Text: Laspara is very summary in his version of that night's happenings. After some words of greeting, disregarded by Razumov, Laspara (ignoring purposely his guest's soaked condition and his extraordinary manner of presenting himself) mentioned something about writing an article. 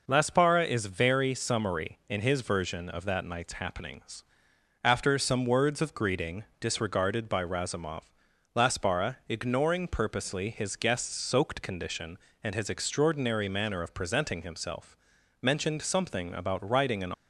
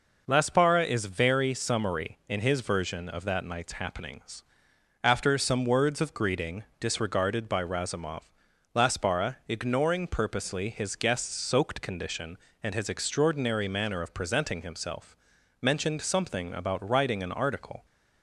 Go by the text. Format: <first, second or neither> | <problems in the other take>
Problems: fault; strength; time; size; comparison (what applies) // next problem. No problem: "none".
second | stops before "article"; at 17.1 s